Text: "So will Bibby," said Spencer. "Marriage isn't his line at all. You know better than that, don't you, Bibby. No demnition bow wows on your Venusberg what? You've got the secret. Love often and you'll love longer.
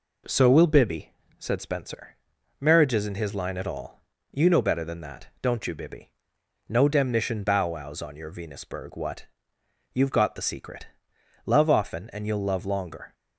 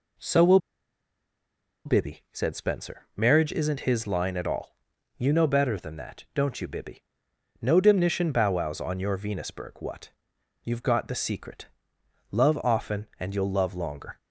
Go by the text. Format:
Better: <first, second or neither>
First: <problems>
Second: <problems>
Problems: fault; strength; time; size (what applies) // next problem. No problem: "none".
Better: first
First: none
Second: pauses between "will" and "Bibby"; strong; at 0.5 s; 1.2 s long